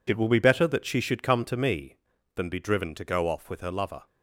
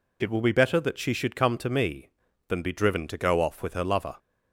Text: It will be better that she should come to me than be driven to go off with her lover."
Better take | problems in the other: second | gets quieter; strong; throughout; 10.5 dB

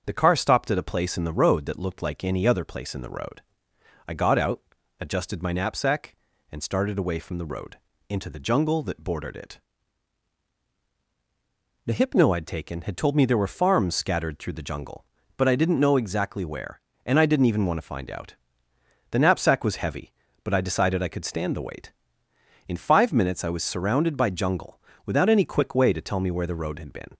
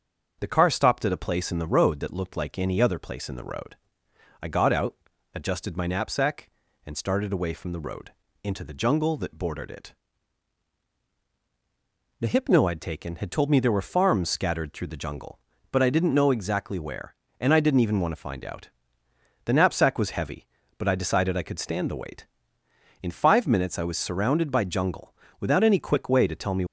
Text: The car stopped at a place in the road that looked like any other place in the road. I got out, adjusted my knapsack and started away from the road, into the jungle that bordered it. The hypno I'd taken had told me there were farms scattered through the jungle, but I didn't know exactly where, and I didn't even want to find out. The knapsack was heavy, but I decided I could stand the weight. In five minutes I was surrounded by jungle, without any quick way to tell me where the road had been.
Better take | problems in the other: first | starts louder than the rest; until 1.4 s; 6.5 dB; also in the first // stops before "where the road had been"; at 26.6 s

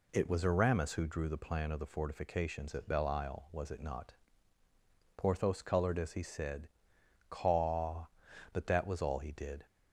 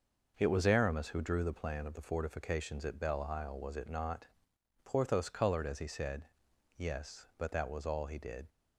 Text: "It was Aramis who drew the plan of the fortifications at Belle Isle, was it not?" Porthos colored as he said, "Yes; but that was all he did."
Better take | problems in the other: second | says "Caw" for "Yes"; at 7.2 s

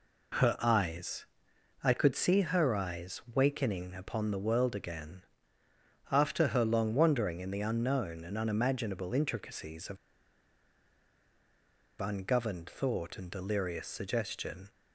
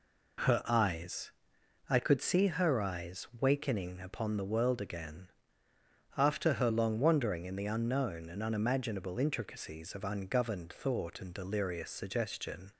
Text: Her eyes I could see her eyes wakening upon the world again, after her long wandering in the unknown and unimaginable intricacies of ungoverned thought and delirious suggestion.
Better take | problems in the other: second | pauses between "eyes" and "I"; noticeable; at 1.2 s; 0.56 s long; noticeable in the second // pauses between "of" and "ungoverned"; strong; at 9.9 s; 2.0 s long

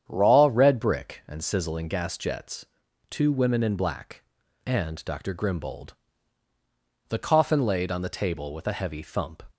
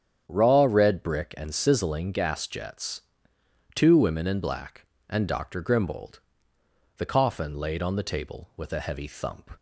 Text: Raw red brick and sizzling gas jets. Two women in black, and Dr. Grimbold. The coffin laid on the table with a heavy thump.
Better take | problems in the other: neither | starts louder than the rest; strong; the same in both

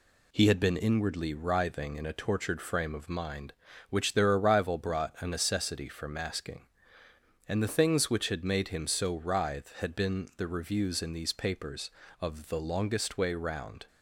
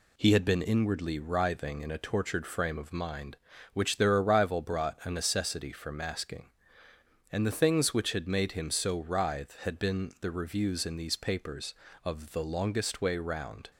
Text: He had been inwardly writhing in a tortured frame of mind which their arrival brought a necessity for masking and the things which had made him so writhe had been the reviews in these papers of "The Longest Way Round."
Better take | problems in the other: neither | none

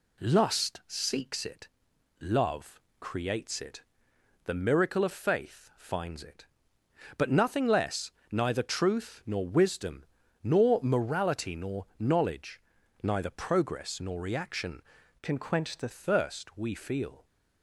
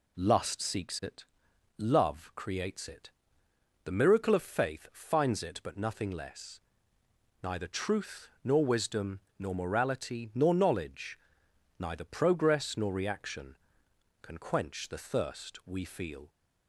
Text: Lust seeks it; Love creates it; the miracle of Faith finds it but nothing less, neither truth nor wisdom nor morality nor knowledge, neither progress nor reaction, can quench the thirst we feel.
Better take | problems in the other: second | pauses between "Love" and "creates"; slight; at 2.8 s; 0.18 s long // pauses between "wisdom" and "nor"; at 10.0 s; 0.38 s long; slight in the second // changes voice from "can" to "the"; from 15.2 to 15.8 s; 0.6 s long

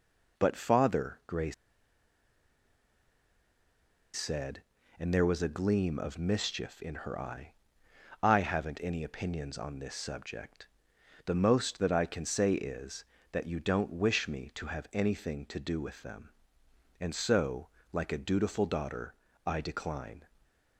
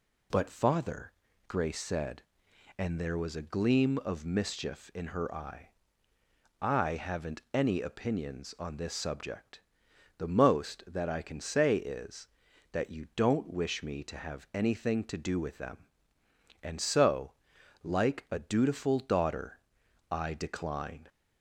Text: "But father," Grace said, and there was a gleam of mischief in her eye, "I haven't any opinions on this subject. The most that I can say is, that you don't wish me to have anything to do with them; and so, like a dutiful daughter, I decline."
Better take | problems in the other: second | pauses between "Grace" and "said"; strong; at 1.5 s; 2.6 s long // stays silent after the last word; slight; from 20.2 s on; 0.5 s long

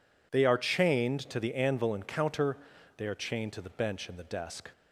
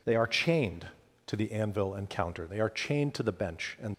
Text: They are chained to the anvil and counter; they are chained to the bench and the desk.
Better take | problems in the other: first | stops before "the desk"; at 3.9 s

